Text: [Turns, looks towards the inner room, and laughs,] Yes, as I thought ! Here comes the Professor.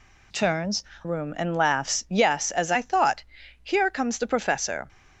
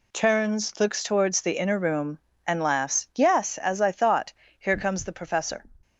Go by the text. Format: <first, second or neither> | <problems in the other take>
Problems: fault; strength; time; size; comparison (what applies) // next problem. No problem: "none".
second | skips "looks towards the inner"; at 0.9 s